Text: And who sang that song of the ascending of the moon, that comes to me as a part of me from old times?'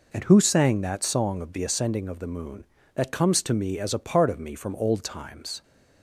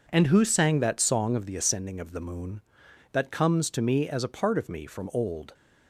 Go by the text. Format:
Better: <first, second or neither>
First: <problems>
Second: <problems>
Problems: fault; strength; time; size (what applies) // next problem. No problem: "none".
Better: first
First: none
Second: stops before "times"; at 5.5 s